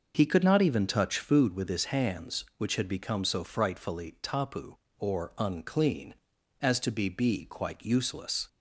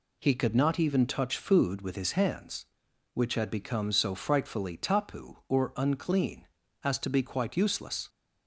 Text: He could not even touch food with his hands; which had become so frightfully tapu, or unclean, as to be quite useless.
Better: second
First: says "be" twice; at 7.0 s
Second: none

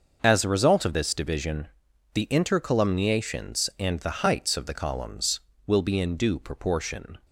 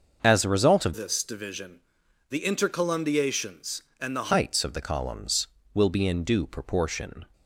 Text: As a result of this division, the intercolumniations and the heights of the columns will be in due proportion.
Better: first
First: starts louder than the rest; until 1.2 s; 6.5 dB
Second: starts louder than the rest; until 1.2 s; 6.5 dB // changes voice from "this" to "the"; from 0.9 to 4.2 s; 3.3 s long

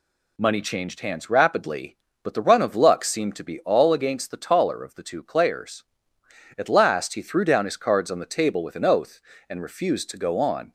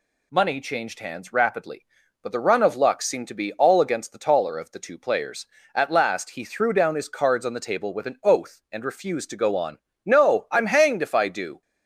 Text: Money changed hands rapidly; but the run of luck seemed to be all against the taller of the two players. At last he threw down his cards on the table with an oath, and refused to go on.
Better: first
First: none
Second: goes on to say "No I'm hanged if I do"; from 10.0 s on; 1.5 s long

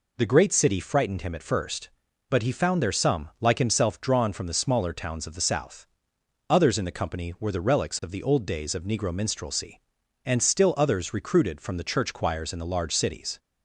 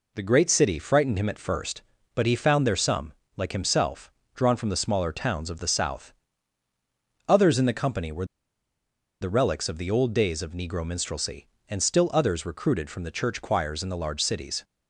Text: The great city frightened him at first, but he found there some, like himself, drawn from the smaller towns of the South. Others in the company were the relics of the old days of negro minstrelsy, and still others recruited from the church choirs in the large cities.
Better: first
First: none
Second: pauses between "were" and "the"; noticeable; at 8.2 s; 0.95 s long

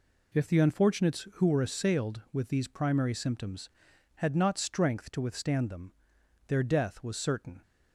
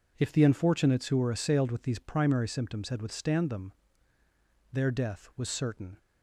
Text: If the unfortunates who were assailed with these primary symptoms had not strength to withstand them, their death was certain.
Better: first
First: none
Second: skips "not strength to"; at 3.0 s

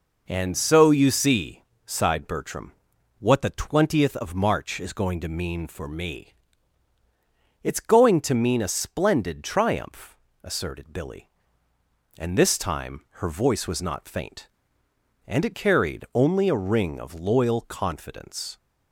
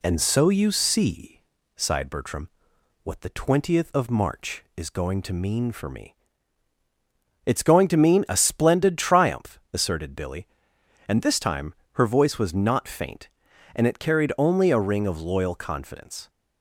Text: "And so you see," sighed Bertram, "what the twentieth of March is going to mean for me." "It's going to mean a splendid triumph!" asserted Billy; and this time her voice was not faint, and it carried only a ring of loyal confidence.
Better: neither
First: pauses between "time" and "her"; slight; at 13.0 s; 0.18 s long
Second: pauses between "time" and "her"; slight; at 11.7 s; 0.20 s long

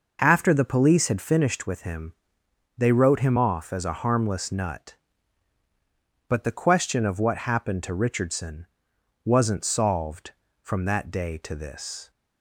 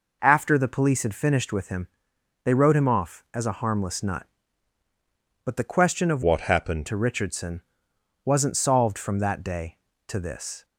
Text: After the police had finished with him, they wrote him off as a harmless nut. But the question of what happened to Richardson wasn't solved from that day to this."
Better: first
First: pauses between "Richardson" and "wasn't"; noticeable; at 8.6 s; 0.58 s long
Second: changes voice from "what" to "happened"; from 6.2 to 6.8 s; 0.6 s long // pauses between "Richardson" and "wasn't"; noticeable; at 7.6 s; 0.64 s long

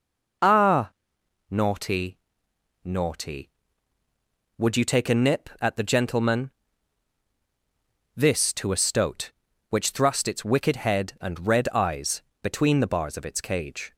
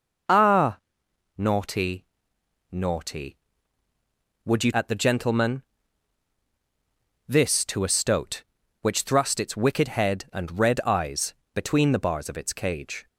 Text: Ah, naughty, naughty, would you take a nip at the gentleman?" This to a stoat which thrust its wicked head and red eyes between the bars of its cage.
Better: first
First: pauses between "eyes" and "between"; slight; at 12.2 s; 0.22 s long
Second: skips "take a nip"; at 4.7 s // pauses between "eyes" and "between"; slight; at 11.3 s; 0.22 s long

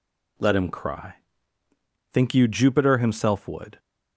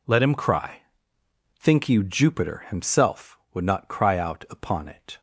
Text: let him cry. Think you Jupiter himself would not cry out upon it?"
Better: second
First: stops before "not cry out upon it"; at 3.7 s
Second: none

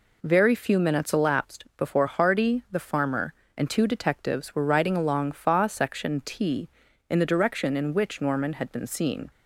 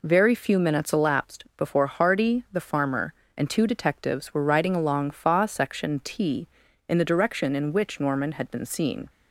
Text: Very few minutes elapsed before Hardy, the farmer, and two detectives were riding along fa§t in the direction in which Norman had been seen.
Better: neither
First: none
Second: none

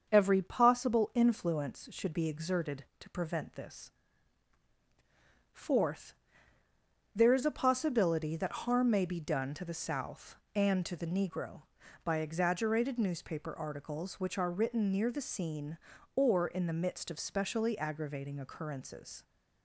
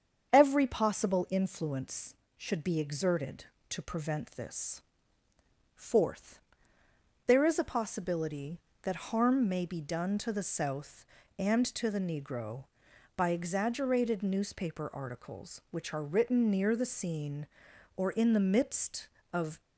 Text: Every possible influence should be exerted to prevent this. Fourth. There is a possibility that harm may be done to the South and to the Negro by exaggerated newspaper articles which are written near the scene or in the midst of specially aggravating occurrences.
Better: first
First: starts louder than the rest; until 1.1 s; 6.5 dB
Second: starts louder than the rest; strong; until 1.3 s; 7.5 dB // stops before "specially aggravating occurrences"; at 19.5 s

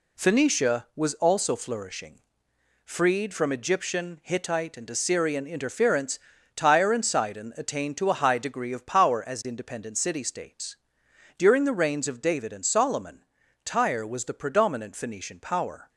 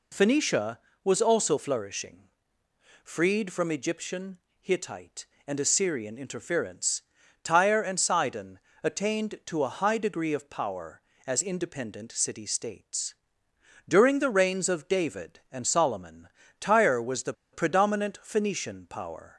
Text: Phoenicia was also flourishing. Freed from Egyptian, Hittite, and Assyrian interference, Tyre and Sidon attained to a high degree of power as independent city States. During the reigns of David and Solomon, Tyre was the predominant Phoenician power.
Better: first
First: none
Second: pauses between "Sidon" and "attained"; slight; at 8.5 s; 0.24 s long // pauses between "the" and "predominant"; slight; at 17.3 s; 0.20 s long

